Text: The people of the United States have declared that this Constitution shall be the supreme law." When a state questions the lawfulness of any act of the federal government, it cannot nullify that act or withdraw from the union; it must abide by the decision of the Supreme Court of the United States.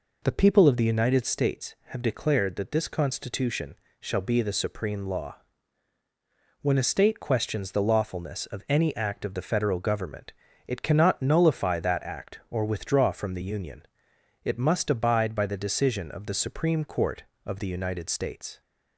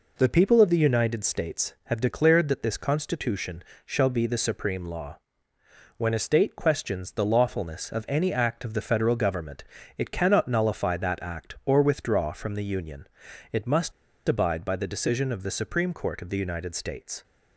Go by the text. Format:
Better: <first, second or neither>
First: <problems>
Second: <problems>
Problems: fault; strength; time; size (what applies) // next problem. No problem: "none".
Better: first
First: pauses between "Constitution" and "shall"; slight; at 3.7 s; 0.24 s long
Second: pauses between "Constitution" and "shall"; slight; at 3.6 s; 0.22 s long // pauses between "must" and "abide"; slight; at 13.9 s; 0.34 s long